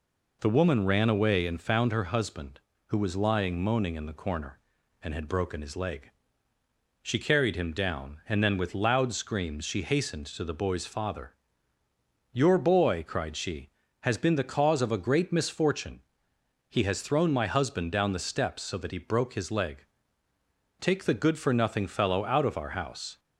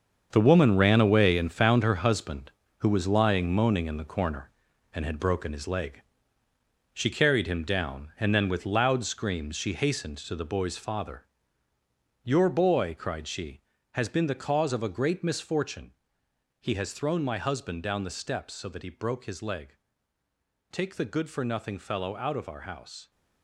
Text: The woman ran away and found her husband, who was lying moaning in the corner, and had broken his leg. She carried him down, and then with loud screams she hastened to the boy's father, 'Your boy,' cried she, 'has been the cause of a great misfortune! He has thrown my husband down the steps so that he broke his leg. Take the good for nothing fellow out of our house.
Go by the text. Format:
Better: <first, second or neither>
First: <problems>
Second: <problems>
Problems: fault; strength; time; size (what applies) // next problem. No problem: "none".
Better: first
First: none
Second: gets quieter; strong; throughout; 10.5 dB